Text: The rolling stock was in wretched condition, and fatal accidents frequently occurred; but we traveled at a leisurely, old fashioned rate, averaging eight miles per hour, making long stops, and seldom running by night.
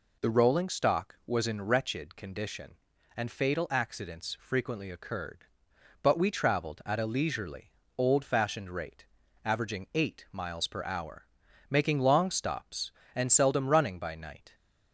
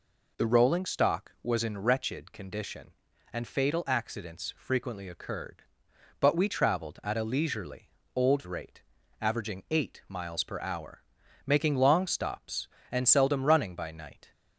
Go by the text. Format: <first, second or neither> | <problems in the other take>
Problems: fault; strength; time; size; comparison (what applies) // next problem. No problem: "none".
first | skips "fashioned"; at 8.4 s